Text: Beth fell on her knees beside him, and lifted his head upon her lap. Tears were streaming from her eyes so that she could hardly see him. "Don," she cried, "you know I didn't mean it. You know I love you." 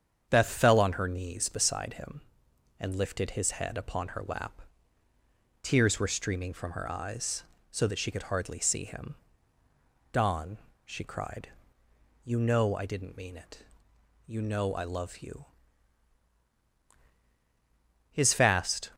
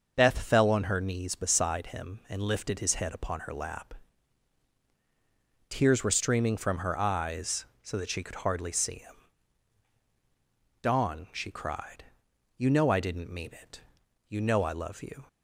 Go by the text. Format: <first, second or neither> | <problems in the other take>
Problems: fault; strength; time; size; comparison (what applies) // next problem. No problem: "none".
second | starts louder than the rest; strong; until 1.3 s; 7.5 dB; also in the second // goes on to say "His fast"; noticeable; from 18.1 s on; 0.80 s long